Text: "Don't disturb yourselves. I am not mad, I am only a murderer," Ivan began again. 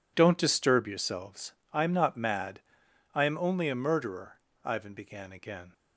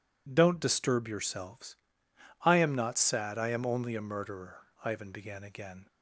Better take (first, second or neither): first